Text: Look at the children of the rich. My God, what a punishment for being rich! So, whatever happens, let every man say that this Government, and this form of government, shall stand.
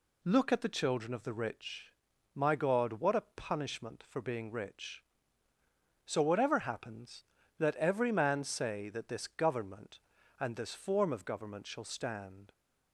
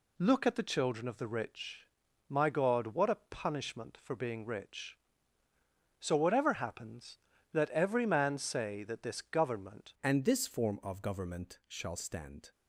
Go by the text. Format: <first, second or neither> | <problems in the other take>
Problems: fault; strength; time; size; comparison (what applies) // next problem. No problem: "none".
first | changes voice at "and"; from 10.0 s on; 2.5 s long